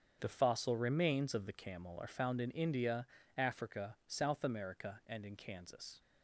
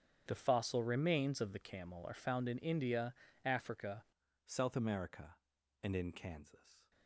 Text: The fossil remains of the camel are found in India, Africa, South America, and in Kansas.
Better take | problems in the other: first | starts louder than the rest; strong; until 1.2 s; 8.5 dB; strong in the first // changes voice at "South"; from 4.4 s on; 2.5 s long

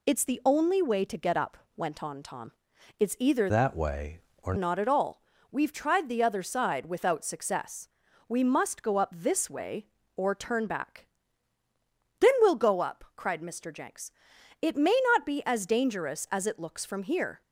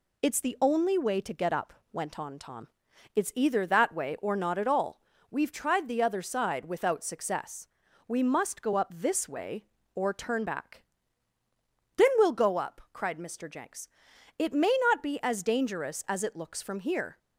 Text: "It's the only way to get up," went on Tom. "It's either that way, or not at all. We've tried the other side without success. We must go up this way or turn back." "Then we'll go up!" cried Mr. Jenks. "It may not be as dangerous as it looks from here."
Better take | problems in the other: second | changes voice from "that" to "or"; from 3.4 to 4.5 s; 1.1 s long

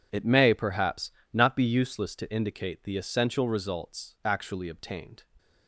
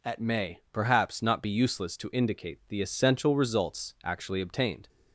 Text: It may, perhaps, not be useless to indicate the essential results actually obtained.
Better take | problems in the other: first | says "At" for "It"; at 0.0 s

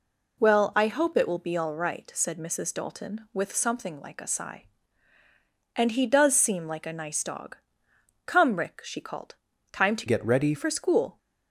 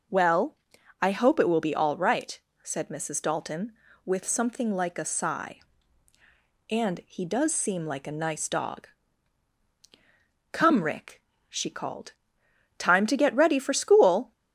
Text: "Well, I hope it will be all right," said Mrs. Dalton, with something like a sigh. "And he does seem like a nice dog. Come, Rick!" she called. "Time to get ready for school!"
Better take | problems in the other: second | changes voice from "get" to "ready"; from 10.0 to 10.5 s; 0.5 s long

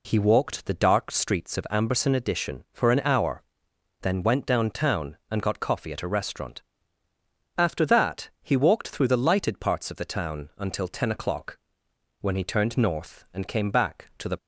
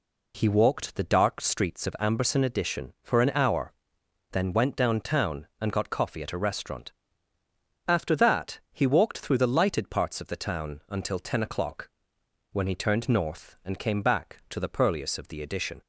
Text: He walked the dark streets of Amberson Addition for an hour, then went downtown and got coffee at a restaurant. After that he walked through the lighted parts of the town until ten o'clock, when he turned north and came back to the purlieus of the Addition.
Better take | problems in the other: second | stops before "purlieus of the Addition"; at 14.3 s

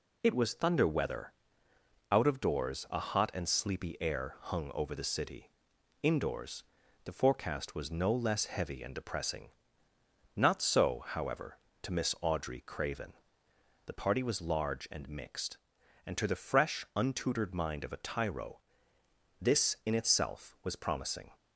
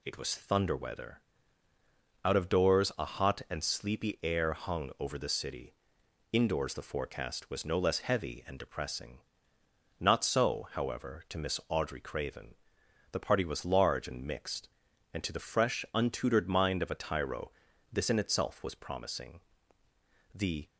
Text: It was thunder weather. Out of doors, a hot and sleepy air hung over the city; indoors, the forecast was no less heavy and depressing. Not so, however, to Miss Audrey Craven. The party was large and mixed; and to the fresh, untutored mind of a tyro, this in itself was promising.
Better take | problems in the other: first | goes on to say "The"; slight; from 20.3 s on; 0.32 s long

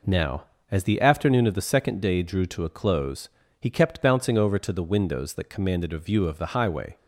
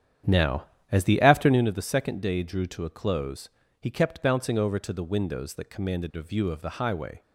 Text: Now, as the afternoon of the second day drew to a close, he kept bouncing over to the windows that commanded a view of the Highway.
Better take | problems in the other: first | starts louder than the rest; strong; until 1.6 s; 9.5 dB

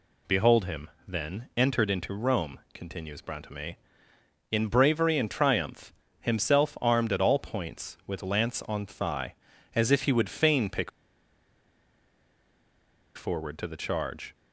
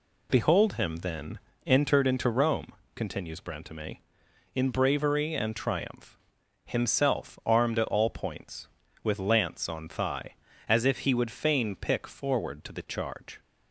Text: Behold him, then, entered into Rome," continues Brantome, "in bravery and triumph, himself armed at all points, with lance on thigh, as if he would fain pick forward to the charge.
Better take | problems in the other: second | pauses between "pick" and "forward"; strong; at 10.8 s; 2.2 s long

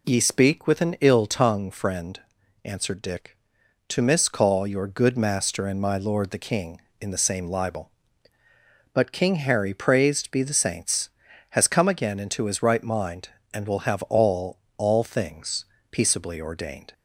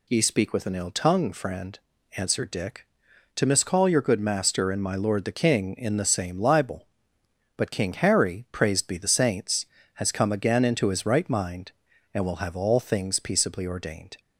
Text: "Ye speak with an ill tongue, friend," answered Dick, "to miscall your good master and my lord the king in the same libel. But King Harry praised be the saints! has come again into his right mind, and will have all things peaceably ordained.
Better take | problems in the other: second | says "all" twice; at 14.7 s // pauses between "things" and "peaceably"; slight; at 15.6 s; 0.26 s long

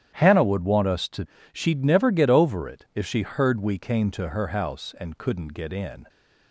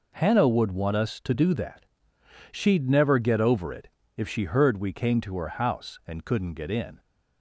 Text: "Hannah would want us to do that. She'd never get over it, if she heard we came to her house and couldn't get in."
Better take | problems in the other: second | starts louder than the rest; strong; until 1.1 s; 10.5 dB // skips "do that"; at 1.3 s

